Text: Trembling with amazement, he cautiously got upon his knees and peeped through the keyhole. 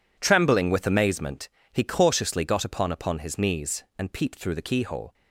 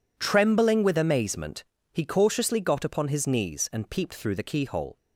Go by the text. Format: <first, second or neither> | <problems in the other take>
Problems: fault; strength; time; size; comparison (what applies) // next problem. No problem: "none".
second | says "upon" twice; at 2.9 s